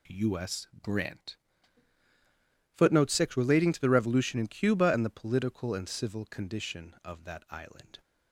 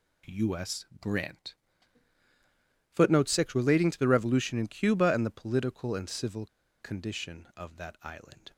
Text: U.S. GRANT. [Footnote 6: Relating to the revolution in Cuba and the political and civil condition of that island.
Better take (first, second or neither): first